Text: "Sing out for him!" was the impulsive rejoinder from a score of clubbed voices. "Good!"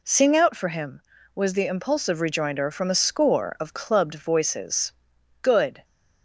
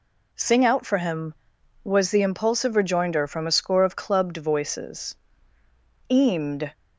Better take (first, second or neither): first